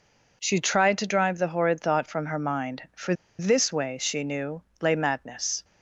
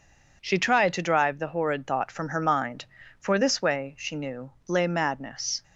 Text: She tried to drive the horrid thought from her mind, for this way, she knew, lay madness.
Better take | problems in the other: second | pauses between "for" and "this"; slight; at 3.1 s; 0.25 s long

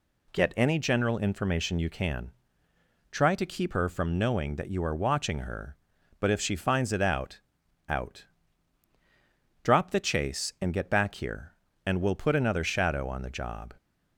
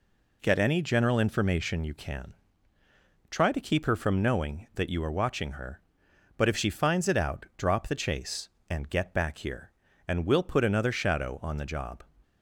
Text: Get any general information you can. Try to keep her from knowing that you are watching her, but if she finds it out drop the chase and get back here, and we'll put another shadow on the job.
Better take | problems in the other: second | says "out" twice; at 7.8 s

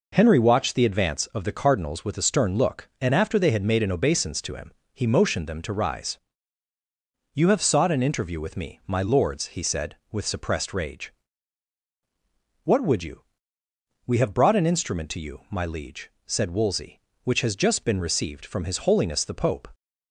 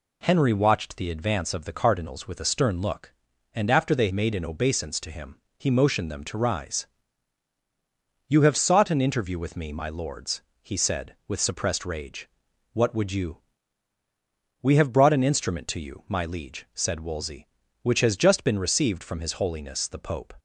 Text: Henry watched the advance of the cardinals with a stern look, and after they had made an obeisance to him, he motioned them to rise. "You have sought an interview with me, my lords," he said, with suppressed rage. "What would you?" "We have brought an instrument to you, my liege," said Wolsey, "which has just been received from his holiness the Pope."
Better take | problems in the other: first | skips "had"; at 4.1 s

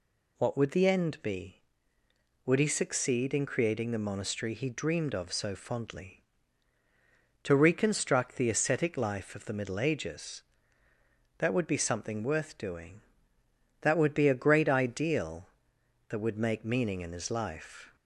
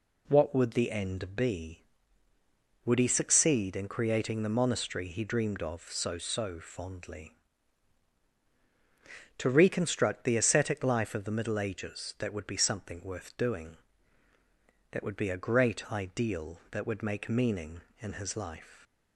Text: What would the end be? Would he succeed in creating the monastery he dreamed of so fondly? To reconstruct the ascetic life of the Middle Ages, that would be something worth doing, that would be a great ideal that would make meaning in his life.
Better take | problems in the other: first | says "so" twice; at 6.1 s

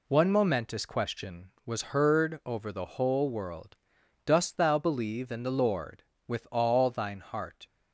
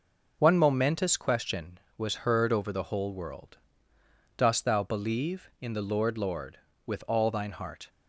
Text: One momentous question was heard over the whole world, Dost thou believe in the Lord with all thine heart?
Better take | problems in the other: first | says "Lord" twice; at 6.1 s

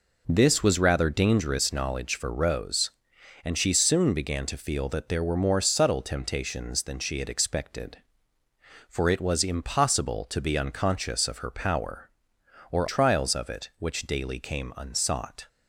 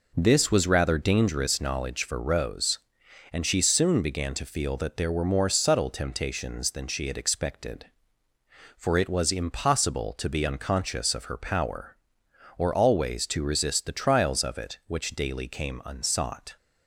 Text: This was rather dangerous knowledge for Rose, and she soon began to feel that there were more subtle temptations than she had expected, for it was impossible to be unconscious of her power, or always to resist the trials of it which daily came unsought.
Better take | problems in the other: second | skips "always to resist the"; at 12.8 s

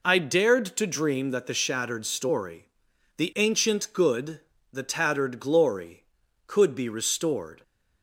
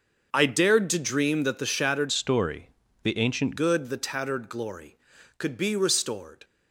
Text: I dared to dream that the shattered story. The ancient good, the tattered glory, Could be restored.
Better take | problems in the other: first | starts louder than the rest; until 1.3 s; 6.5 dB // changes voice from "story" to "ancient"; from 2.0 to 3.5 s; 1.5 s long

